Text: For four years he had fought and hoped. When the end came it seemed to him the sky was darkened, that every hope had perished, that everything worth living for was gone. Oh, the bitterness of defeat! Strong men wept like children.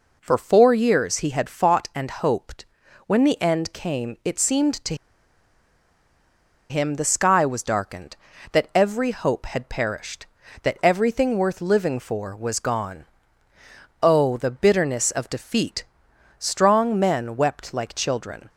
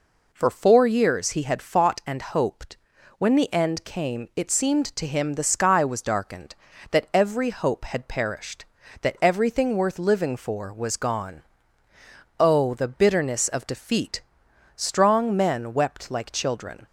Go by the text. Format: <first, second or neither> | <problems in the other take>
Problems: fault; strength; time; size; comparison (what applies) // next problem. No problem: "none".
second | pauses between "to" and "him"; strong; at 4.9 s; 1.7 s long